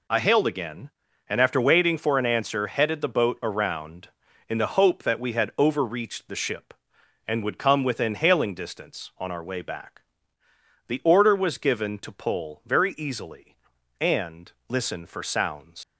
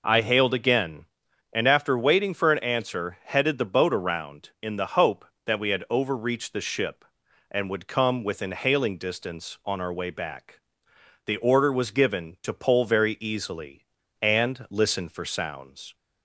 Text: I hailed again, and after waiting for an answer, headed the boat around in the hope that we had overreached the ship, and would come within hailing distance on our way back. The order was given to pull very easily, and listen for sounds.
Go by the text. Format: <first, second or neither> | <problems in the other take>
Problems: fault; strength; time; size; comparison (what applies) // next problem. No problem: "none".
second | pauses between "and" and "listen"; slight; at 14.5 s; 0.18 s long // leaves "sounds" unfinished; at 15.8 s; 120 ms